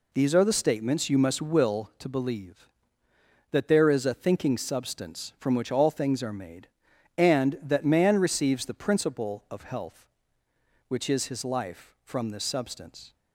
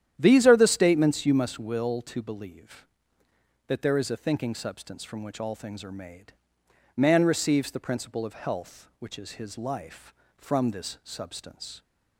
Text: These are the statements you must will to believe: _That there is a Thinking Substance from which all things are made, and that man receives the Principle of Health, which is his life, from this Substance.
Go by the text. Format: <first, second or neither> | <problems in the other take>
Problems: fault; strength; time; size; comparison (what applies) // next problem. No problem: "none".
first | starts louder than the rest; strong; until 1.1 s; 10.5 dB // skips "and that"; at 6.6 s